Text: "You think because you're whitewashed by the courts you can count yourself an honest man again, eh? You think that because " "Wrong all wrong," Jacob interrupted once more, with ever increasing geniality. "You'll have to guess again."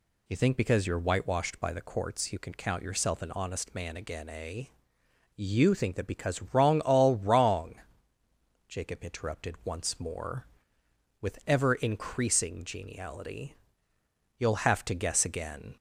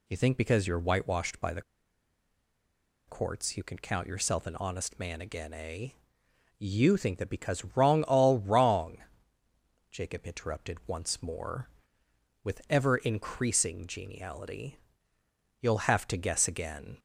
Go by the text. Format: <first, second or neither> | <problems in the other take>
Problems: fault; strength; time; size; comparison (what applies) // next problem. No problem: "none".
first | pauses between "the" and "courts"; strong; at 1.6 s; 1.4 s long